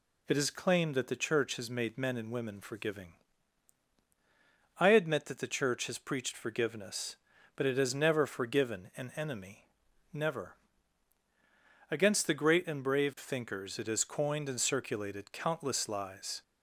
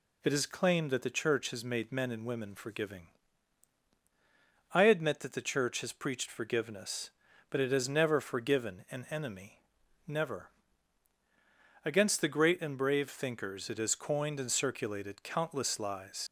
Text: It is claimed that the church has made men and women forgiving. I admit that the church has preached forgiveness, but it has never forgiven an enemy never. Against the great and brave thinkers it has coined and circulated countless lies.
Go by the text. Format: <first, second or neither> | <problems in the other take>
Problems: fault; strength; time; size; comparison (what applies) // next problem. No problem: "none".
first | pauses between "enemy" and "never"; noticeable; at 9.6 s; 0.46 s long; noticeable in the first // leaves "lies" unfinished; at 16.2 s; 60 ms